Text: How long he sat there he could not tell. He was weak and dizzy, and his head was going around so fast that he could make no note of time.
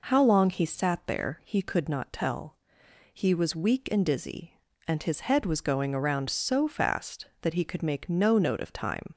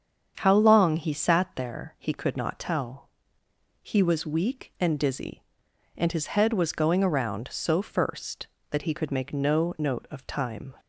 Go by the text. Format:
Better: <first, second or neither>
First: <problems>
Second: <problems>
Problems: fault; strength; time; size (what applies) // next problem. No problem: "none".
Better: first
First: none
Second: starts louder than the rest; strong; until 1.3 s; 7.5 dB // says "first" for "fast"; at 7.8 s